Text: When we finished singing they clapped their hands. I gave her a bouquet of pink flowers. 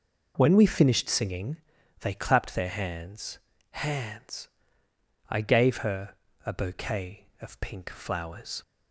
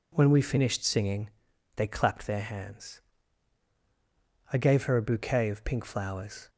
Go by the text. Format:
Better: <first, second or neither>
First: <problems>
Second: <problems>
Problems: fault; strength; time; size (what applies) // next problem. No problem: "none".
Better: second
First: pauses between "singing" and "they"; noticeable; at 1.5 s; 0.46 s long // says "hands" twice; at 3.6 s // pauses between "her" and "a"; slight; at 6.1 s; 0.30 s long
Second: pauses between "singing" and "they"; at 1.3 s; 0.44 s long